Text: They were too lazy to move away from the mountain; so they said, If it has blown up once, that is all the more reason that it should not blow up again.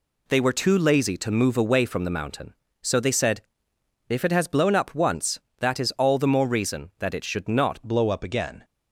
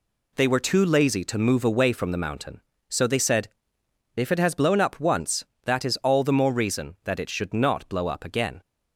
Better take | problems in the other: second | changes voice at "blow"; from 7.8 s on; 0.8 s long

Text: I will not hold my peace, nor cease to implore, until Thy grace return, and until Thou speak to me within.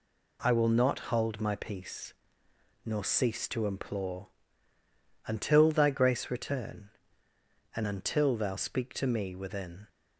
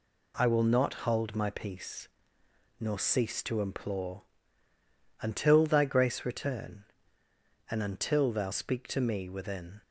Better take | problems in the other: neither | none

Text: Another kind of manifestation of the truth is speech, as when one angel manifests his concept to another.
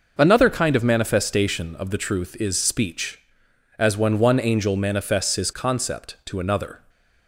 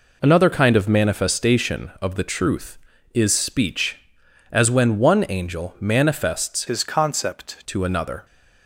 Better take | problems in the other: first | changes voice from "his" to "concept"; from 6.6 to 7.5 s; 0.9 s long

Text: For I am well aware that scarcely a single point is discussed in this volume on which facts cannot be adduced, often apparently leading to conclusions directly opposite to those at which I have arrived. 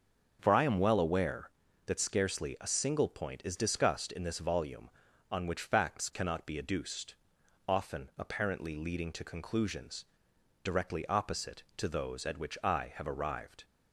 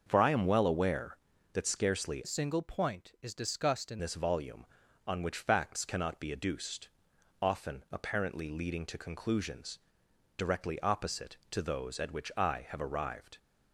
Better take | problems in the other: first | starts louder than the rest; until 1.0 s; 6.5 dB; also in the first // changes voice from "a" to "in"; from 2.2 to 3.9 s; 1.7 s long // pauses between "conclusions" and "directly"; noticeable; at 9.7 s; 0.60 s long; noticeable in the first

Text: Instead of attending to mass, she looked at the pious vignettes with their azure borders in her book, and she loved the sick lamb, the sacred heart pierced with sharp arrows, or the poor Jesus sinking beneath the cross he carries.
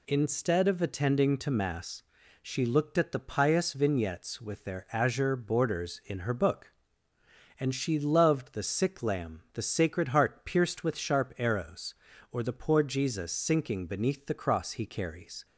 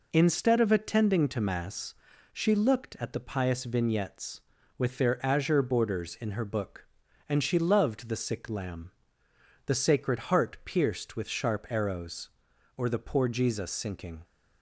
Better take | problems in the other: first | stops before "beneath the cross he carries"; at 14.2 s

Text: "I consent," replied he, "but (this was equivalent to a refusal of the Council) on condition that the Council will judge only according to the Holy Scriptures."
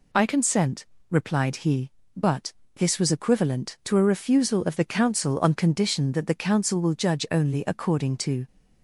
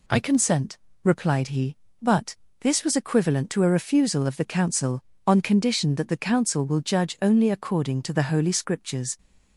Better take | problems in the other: second | stops before "the Holy Scriptures"; at 8.4 s

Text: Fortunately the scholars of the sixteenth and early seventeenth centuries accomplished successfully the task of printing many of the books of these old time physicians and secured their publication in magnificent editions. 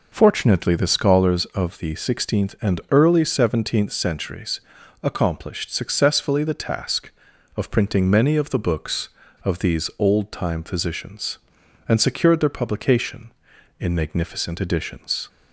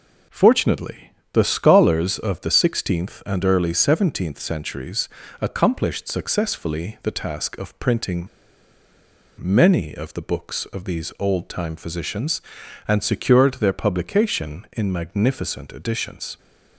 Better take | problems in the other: first | pauses between "Fortunately" and "the"; slight; at 1.0 s; 0.28 s long // pauses between "centuries" and "accomplished"; slight; at 5.0 s; 0.32 s long; also in the first // pauses between "printing" and "many"; at 8.2 s; 1.1 s long

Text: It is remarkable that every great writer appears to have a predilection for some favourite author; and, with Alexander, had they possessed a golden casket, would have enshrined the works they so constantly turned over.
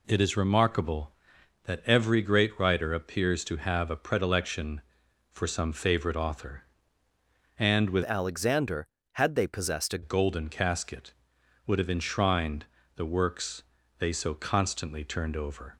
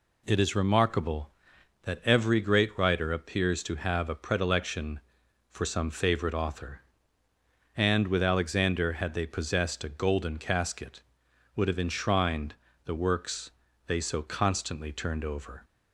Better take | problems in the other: second | changes voice from "Alexander" to "a"; from 8.0 to 10.0 s; 2.0 s long // pauses between "enshrined" and "the"; slight; at 12.6 s; 0.32 s long; slight in the second // pauses between "works" and "they"; at 13.6 s; 0.38 s long; also in the second

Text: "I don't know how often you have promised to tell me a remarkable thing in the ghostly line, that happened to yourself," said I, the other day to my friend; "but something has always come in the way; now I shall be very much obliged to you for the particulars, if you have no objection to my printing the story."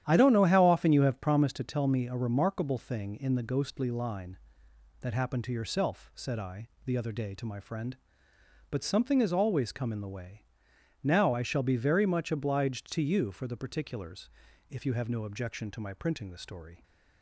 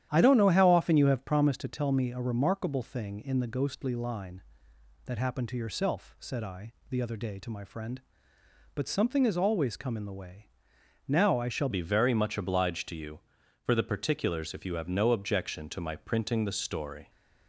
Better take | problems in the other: first | starts louder than the rest; strong; until 1.1 s; 10.5 dB; strong in the first // changes voice at "be"; from 11.7 s on; 5.3 s long

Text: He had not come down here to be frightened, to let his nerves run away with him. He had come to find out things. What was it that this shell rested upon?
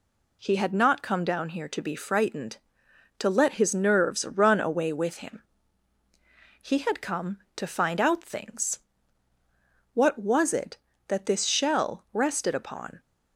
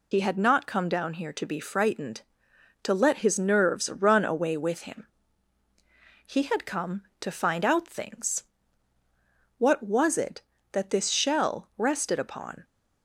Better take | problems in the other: first | loses the start of "He"; at 0.1 s; 70 ms

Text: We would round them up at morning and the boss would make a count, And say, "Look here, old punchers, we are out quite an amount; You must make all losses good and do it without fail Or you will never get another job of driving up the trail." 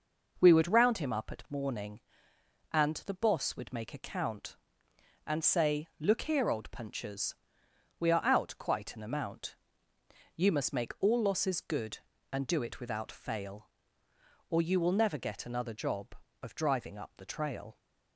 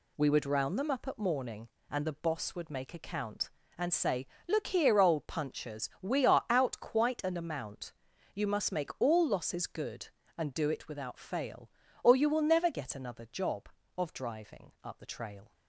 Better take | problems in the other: second | says "him" for "them"; at 0.9 s

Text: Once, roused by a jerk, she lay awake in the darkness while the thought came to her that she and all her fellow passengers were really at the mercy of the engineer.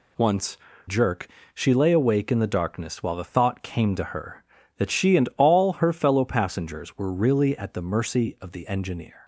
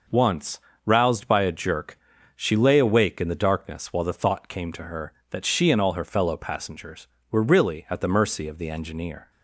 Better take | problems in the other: second | skips "roused by a"; at 0.7 s

